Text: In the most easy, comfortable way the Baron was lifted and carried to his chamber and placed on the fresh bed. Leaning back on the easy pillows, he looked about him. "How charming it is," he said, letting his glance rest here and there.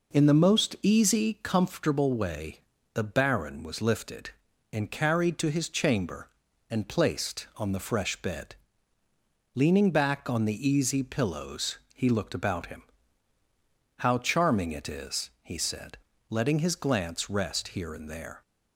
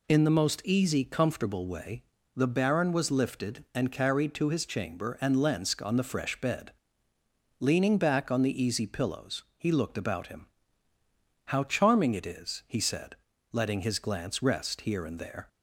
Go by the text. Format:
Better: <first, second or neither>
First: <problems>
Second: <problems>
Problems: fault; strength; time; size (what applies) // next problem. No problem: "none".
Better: first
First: pauses between "way" and "the"; slight; at 2.5 s; 0.32 s long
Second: pauses between "way" and "the"; slight; at 2.0 s; 0.34 s long // says "lensk" for "placed"; at 5.3 s